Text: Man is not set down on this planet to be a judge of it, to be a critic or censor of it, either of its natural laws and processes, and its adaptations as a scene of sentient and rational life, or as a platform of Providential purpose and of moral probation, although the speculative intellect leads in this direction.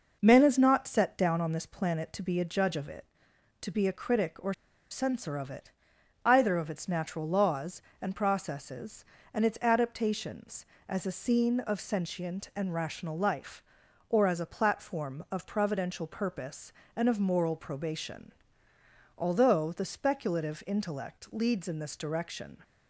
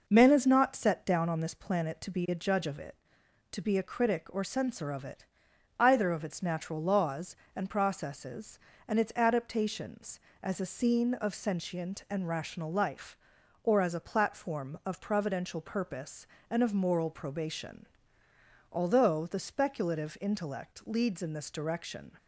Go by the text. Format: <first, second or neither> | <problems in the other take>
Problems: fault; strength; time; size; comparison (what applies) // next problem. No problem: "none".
second | pauses between "or" and "censor"; at 4.5 s; 0.38 s long